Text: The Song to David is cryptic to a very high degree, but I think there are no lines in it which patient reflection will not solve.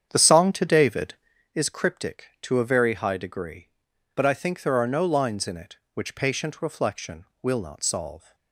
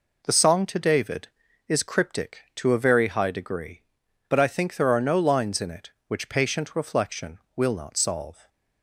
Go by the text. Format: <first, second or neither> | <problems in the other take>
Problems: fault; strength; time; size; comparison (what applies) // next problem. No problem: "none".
second | starts louder than the rest; strong; until 1.5 s; 8.5 dB